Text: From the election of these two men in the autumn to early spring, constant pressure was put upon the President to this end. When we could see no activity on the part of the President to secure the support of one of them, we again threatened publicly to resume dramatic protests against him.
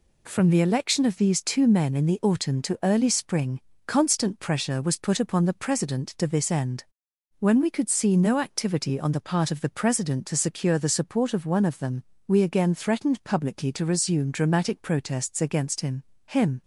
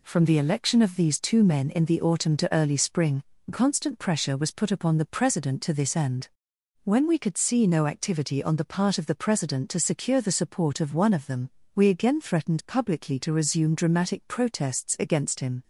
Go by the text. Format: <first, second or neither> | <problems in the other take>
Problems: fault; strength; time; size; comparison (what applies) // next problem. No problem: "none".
second | says "him" twice; at 16.2 s